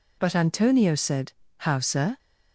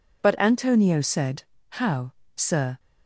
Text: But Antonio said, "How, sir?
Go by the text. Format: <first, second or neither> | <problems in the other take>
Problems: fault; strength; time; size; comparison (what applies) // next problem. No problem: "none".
neither | none